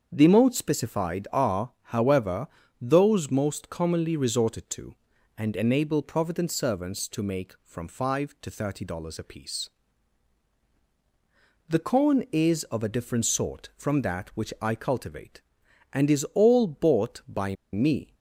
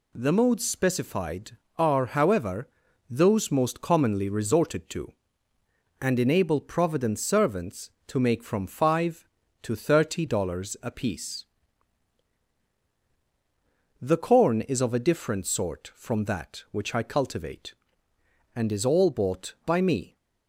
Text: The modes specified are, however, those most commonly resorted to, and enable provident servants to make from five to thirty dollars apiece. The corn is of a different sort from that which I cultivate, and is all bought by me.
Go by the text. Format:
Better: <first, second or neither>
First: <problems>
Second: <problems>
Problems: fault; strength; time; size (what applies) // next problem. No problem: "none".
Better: second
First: starts louder than the rest; until 1.1 s; 7 dB // pauses between "by" and "me"; slight; at 17.5 s; 0.17 s long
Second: none